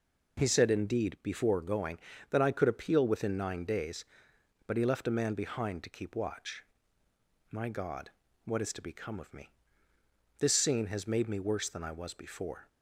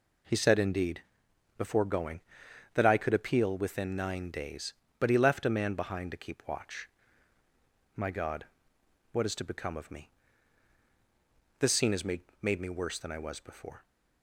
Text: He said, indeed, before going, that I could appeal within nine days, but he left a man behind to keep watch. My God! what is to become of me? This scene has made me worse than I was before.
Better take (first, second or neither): first